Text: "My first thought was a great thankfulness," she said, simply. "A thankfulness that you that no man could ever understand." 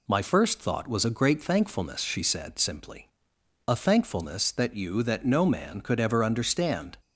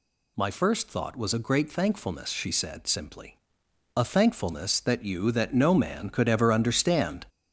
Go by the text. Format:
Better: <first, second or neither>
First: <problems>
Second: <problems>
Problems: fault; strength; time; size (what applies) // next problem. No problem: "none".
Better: first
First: none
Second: gets louder; noticeable; throughout; 5 dB